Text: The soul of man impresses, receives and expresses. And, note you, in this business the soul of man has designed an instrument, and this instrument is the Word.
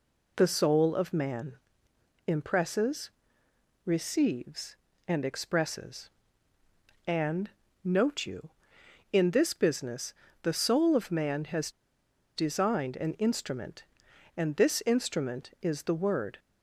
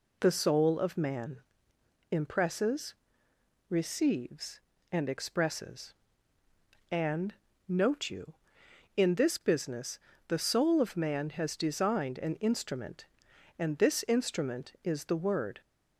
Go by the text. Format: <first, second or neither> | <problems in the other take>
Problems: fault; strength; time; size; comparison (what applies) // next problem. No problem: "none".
second | pauses between "man" and "impresses"; noticeable; at 1.5 s; 0.70 s long; noticeable in the second // pauses between "business" and "the"; slight; at 10.1 s; 0.28 s long; slight in the second // pauses between "has" and "designed"; noticeable; at 11.7 s; 0.65 s long